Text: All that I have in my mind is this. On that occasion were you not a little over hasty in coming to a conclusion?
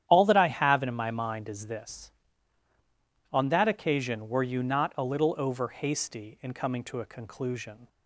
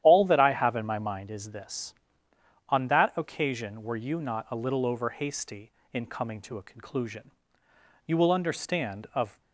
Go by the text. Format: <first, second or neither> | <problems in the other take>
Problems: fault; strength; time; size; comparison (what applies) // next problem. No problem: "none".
first | starts louder than the rest; strong; until 1.0 s; 11 dB; strong in the first // goes on to say "You will understand of"; from 8.0 s on; 1.3 s long